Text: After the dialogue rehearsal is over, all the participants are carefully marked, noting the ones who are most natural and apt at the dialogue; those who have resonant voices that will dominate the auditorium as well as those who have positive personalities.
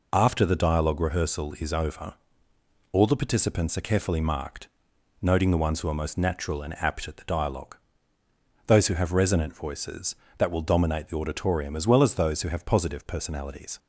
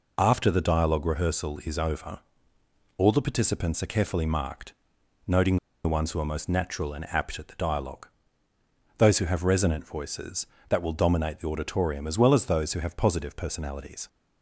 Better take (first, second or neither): first